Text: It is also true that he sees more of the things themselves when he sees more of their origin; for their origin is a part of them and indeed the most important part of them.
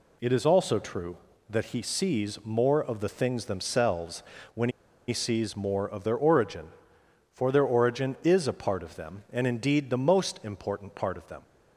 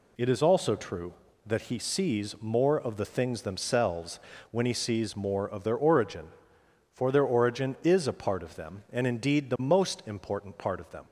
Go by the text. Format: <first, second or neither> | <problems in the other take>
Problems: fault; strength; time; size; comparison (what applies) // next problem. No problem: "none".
second | pauses between "themselves" and "when"; slight; at 4.2 s; 0.32 s long; slight in the second // pauses between "when" and "he"; at 4.6 s; 0.38 s long